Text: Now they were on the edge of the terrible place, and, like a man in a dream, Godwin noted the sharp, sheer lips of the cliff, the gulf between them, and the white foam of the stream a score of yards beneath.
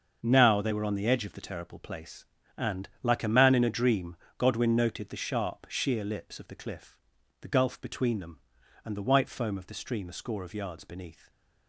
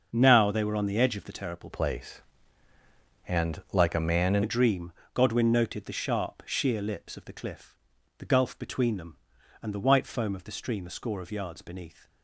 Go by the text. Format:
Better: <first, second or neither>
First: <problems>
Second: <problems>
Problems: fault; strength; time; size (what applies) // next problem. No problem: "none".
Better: first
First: starts louder than the rest; until 1.2 s; 6.5 dB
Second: starts louder than the rest; until 1.1 s; 6.5 dB // changes voice from "place" to "in"; from 1.7 to 4.4 s; 2.7 s long